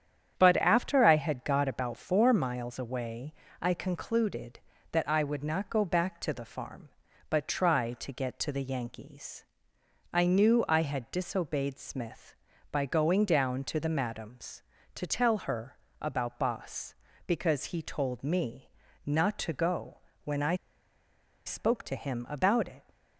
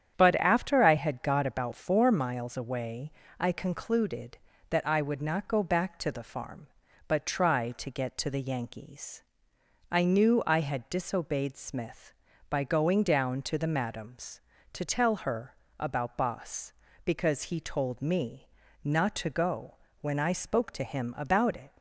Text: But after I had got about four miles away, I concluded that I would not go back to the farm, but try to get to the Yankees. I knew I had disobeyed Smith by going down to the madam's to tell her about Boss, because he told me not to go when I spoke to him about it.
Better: second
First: starts louder than the rest; strong; until 1.4 s; 8.5 dB // pauses between "her" and "about"; slight; at 15.7 s; 0.24 s long // pauses between "me" and "not"; slight; at 18.6 s; 0.36 s long // pauses between "go" and "when"; slight; at 19.9 s; 0.26 s long // pauses between "I" and "spoke"; noticeable; at 20.5 s; 0.91 s long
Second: starts louder than the rest; strong; until 1.2 s; 8.5 dB // pauses between "her" and "about"; slight; at 15.5 s; 0.24 s long // pauses between "me" and "not"; slight; at 18.4 s; 0.36 s long // pauses between "go" and "when"; slight; at 19.7 s; 0.26 s long

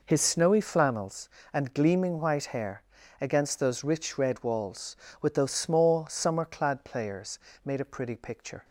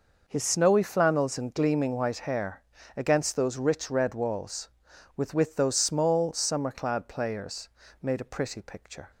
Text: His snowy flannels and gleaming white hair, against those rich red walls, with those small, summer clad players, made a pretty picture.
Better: first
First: none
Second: says "with" twice; at 5.3 s

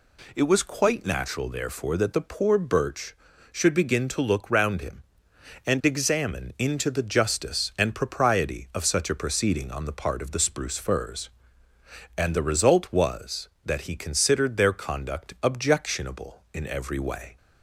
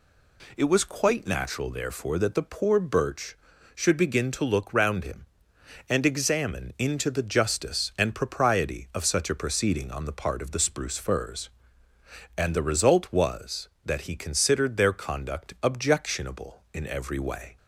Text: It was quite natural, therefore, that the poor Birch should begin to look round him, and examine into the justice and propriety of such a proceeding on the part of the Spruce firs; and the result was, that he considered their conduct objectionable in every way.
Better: neither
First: none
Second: none

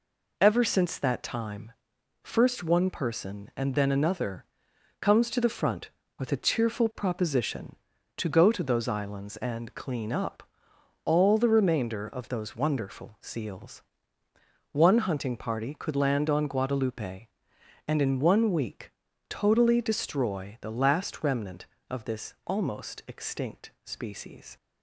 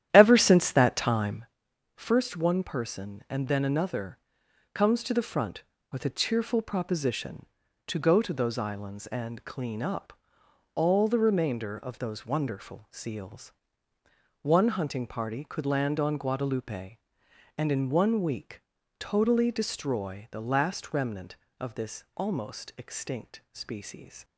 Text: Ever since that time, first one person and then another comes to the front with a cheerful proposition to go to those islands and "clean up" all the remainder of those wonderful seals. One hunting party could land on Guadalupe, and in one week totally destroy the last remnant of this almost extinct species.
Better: first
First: pauses between "another" and "comes"; noticeable; at 4.4 s; 0.56 s long // pauses between "up" and "all"; noticeable; at 10.4 s; 0.62 s long // pauses between "week" and "totally"; slight; at 18.9 s; 0.36 s long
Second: starts louder than the rest; strong; until 1.5 s; 11 dB // pauses between "another" and "comes"; noticeable; at 4.1 s; 0.56 s long // pauses between "up" and "all"; noticeable; at 10.1 s; 0.62 s long // pauses between "week" and "totally"; slight; at 18.6 s; 0.36 s long

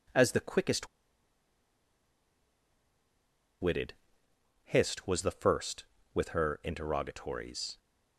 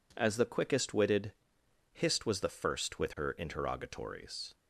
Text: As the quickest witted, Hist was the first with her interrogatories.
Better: second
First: pauses between "quickest" and "witted"; strong; at 0.8 s; 2.7 s long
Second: none

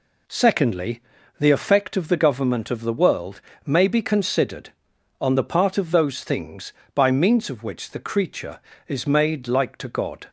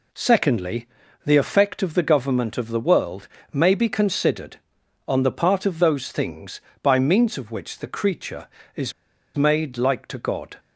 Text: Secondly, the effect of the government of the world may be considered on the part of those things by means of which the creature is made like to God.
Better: first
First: pauses between "world" and "may"; slight; at 3.4 s; 0.26 s long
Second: pauses between "world" and "may"; slight; at 3.2 s; 0.26 s long // pauses between "is" and "made"; at 8.9 s; 0.44 s long

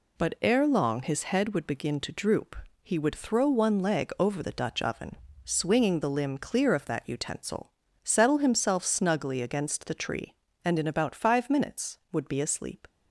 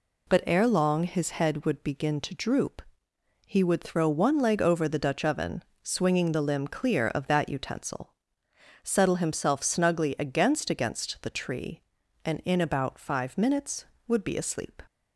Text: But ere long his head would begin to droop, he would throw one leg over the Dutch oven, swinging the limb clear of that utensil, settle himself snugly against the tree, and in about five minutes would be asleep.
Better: first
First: none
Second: says "against" twice; at 10.7 s

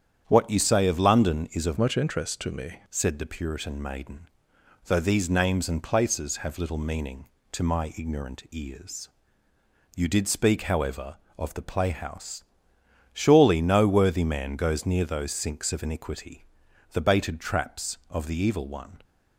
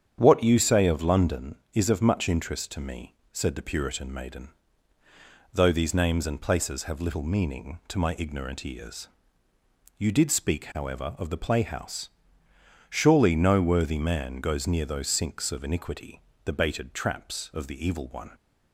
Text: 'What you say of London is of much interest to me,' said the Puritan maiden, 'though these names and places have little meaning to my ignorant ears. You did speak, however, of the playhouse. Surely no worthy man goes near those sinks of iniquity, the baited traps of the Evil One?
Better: second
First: starts louder than the rest; strong; until 1.2 s; 8.5 dB // changes voice from "much" to "me"; from 1.7 to 2.7 s; 1.0 s long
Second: starts louder than the rest; strong; until 1.2 s; 8.5 dB

